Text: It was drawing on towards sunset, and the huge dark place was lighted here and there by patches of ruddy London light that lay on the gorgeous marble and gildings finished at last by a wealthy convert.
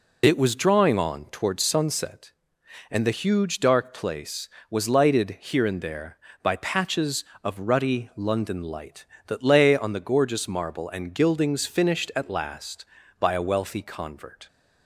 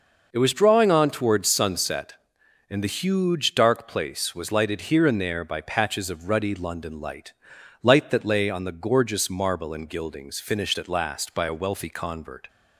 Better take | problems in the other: first | says "light" twice; at 7.8 s

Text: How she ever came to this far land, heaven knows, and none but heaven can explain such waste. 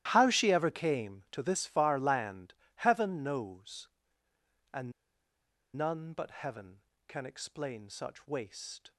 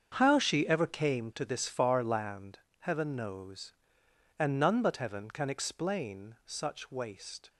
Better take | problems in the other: second | starts louder than the rest; strong; until 1.1 s; 13.5 dB; strong in the second // pauses between "and" and "none"; noticeable; at 4.9 s; 0.83 s long

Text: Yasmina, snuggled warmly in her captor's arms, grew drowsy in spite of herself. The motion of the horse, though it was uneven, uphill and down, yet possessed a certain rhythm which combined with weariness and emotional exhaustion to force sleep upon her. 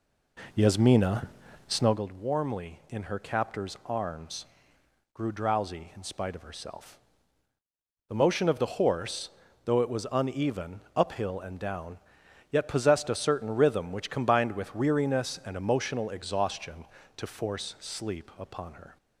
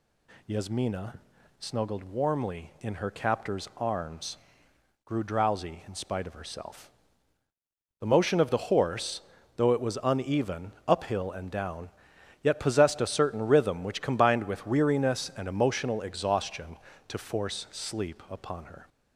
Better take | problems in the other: second | starts louder than the rest; until 2.1 s; 3.5 dB

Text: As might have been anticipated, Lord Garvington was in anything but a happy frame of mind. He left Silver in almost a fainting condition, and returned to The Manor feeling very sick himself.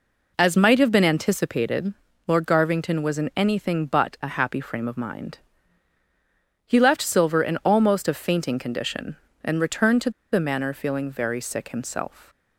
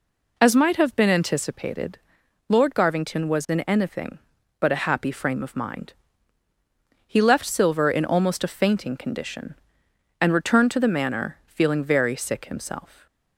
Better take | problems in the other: second | pauses between "to" and "The"; slight; at 10.0 s; 0.22 s long

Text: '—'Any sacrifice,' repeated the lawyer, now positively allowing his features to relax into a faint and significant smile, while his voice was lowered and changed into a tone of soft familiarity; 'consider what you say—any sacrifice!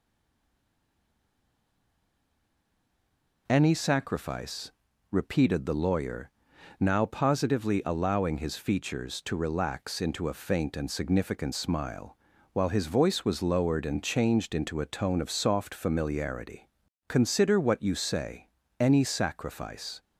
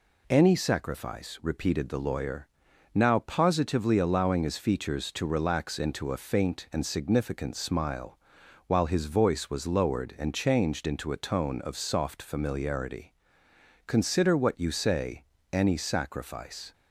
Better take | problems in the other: second | stays silent before the first word; strong; until 3.4 s; 3.4 s long

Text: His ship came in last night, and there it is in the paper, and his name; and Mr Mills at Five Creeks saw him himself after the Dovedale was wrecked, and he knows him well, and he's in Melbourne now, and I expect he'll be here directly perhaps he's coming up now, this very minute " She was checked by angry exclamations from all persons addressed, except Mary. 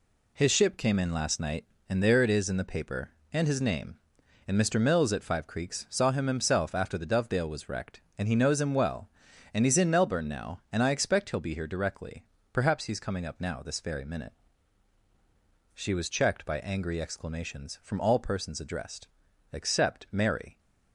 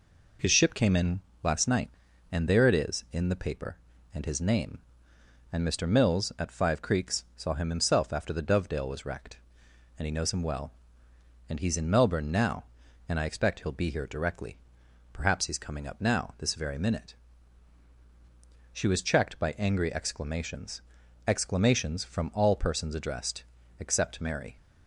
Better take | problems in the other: first | pauses between "in" and "last"; slight; at 1.2 s; 0.22 s long // pauses between "directly" and "perhaps"; noticeable; at 14.5 s; 0.56 s long; slight in the first // says "exclamations" twice; at 21.2 s

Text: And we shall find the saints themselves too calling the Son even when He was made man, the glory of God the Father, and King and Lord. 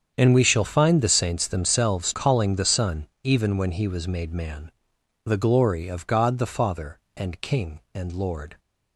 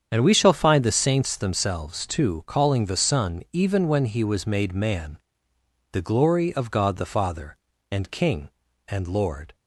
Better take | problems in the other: second | starts louder than the rest; strong; until 1.1 s; 7.5 dB; strong in the second // skips "too"; at 2.1 s // pauses between "Son" and "even"; slight; at 3.0 s; 0.16 s long

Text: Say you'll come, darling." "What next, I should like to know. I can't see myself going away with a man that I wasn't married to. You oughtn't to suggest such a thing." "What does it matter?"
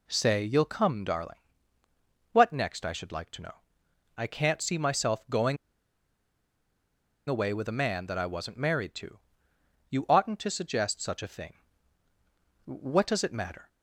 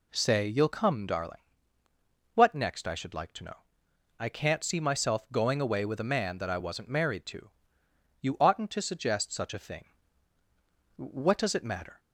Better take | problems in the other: second | pauses between "going" and "away"; strong; at 5.5 s; 1.7 s long

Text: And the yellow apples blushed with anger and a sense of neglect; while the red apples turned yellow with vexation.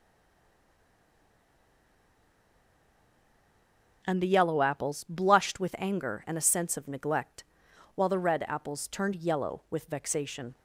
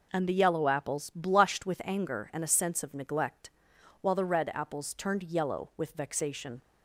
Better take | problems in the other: second | stays silent before the first word; strong; until 4.0 s; 4.0 s long

